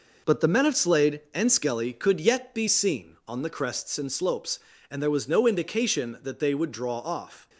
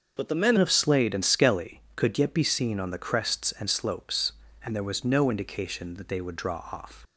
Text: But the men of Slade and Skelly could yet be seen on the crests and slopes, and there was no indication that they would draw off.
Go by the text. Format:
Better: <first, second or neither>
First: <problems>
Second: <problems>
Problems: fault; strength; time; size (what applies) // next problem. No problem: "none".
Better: first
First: none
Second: starts louder than the rest; until 1.1 s; 6.5 dB // changes voice at "of"; from 0.5 s on; 6.5 s long